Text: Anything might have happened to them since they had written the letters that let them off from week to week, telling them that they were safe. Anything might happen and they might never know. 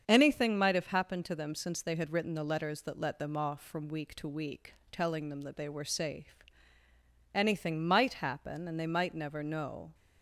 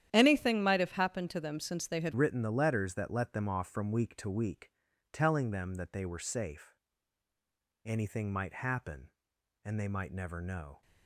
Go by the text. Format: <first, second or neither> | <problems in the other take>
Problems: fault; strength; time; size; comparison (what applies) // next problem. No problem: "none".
first | starts louder than the rest; strong; until 1.1 s; 10.5 dB; strong in the first // changes voice at "written"; from 2.1 s on; 8.7 s long